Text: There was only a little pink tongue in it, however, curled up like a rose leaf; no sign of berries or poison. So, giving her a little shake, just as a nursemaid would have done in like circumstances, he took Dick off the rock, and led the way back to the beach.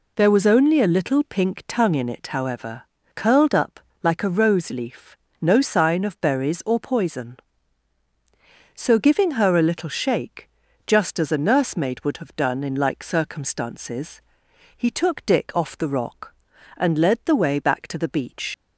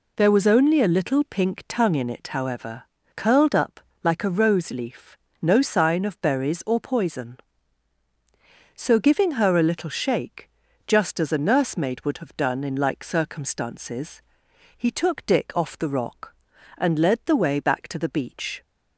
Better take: second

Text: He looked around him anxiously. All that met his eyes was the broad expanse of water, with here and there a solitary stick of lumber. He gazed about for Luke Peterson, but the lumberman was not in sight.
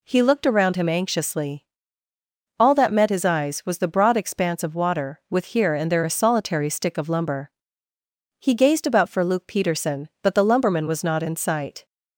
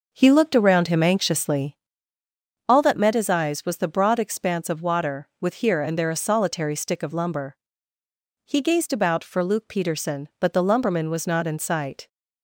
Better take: first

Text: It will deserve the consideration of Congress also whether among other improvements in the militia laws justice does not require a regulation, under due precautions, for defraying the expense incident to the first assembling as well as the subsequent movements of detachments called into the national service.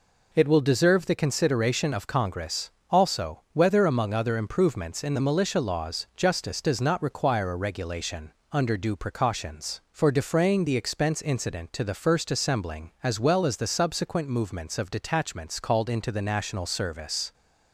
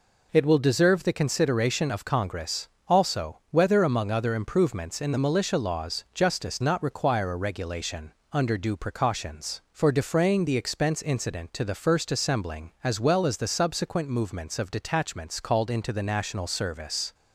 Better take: first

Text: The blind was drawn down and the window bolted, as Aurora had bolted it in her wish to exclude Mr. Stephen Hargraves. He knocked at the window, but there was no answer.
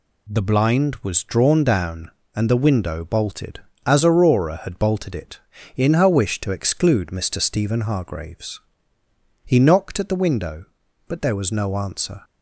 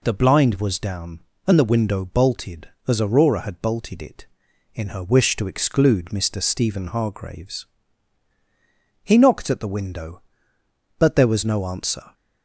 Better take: first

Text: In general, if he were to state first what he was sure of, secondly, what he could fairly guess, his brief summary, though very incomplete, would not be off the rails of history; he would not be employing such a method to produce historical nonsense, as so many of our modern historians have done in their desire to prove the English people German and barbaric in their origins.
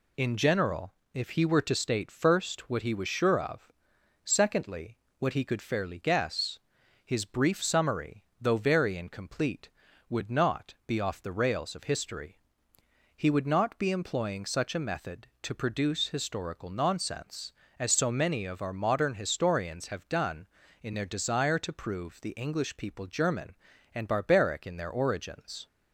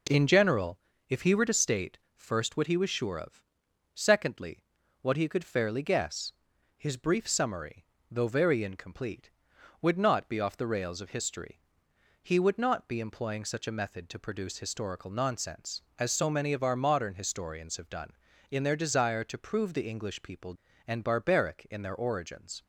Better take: first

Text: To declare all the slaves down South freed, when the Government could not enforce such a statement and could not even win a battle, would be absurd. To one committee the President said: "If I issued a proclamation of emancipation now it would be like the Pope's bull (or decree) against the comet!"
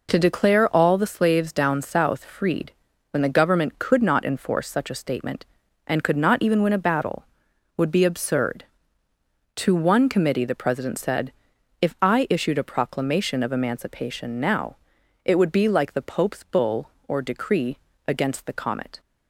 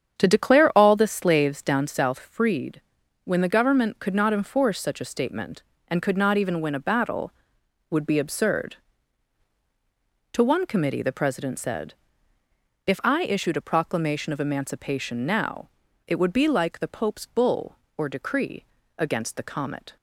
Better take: first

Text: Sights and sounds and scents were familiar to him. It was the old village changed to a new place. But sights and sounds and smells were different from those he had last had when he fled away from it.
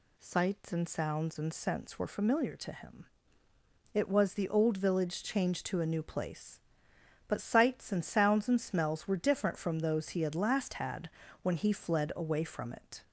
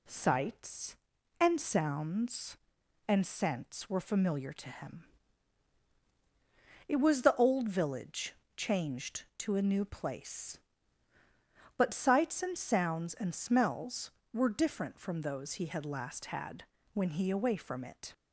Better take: first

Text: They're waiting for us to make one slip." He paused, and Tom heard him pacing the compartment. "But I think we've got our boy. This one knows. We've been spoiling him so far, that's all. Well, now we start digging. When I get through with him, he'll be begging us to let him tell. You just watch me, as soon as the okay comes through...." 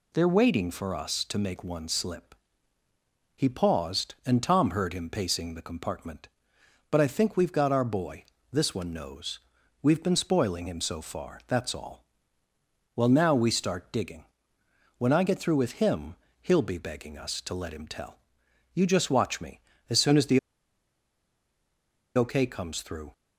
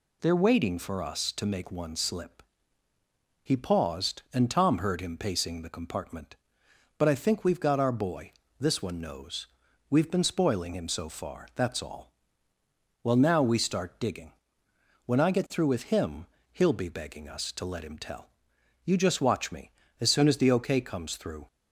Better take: second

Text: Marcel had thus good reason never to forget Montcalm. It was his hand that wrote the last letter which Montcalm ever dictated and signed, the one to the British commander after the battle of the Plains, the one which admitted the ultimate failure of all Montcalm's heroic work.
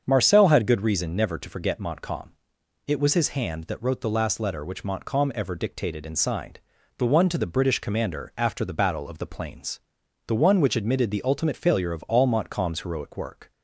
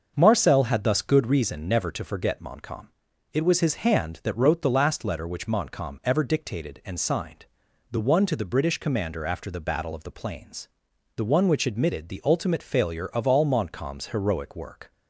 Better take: second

